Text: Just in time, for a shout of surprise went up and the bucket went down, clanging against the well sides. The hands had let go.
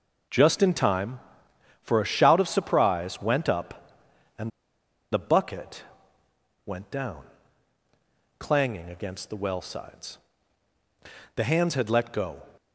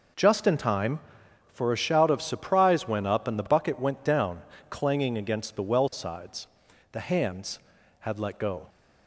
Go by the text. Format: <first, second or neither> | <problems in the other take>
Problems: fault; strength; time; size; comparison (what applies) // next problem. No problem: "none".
second | pauses between "and" and "the"; noticeable; at 4.5 s; 0.63 s long // pauses between "bucket" and "went"; noticeable; at 5.8 s; 0.82 s long